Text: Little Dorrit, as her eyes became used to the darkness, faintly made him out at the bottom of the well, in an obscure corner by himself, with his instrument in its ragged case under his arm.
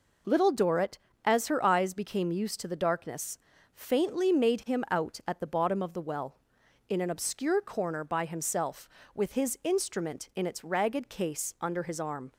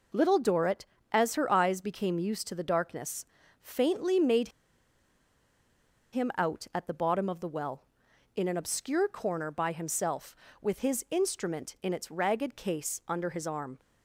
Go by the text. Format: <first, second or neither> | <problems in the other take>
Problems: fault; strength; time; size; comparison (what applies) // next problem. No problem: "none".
first | pauses between "made" and "him"; strong; at 4.4 s; 1.6 s long